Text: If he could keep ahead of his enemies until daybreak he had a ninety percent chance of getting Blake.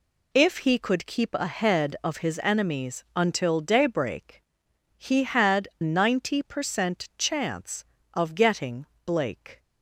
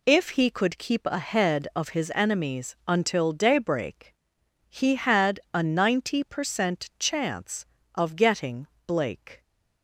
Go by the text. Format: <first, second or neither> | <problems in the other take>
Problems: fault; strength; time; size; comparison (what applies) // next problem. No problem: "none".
second | pauses between "daybreak" and "he"; noticeable; at 4.4 s; 0.52 s long; noticeable in the second // skips "a"; at 5.7 s // pauses between "getting" and "Blake"; slight; at 8.8 s; 0.20 s long; slight in the second